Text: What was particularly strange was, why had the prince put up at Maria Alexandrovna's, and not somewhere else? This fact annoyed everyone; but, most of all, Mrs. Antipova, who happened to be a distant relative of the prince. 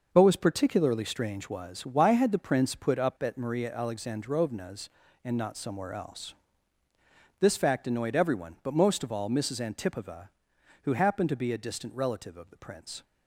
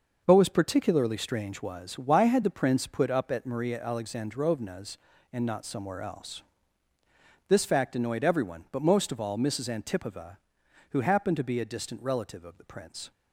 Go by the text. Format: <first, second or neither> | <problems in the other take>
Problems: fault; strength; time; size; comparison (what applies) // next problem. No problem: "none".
neither | none